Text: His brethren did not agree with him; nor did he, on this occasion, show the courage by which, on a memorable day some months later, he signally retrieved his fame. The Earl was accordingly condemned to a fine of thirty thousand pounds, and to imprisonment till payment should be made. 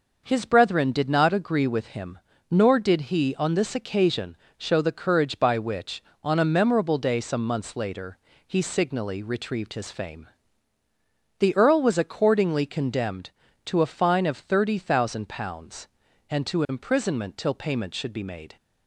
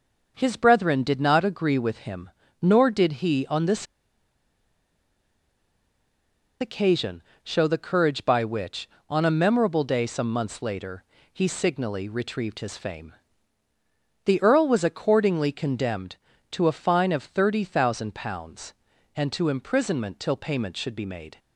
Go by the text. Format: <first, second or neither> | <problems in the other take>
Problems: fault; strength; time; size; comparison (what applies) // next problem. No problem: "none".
first | pauses between "this" and "occasion"; strong; at 3.8 s; 2.7 s long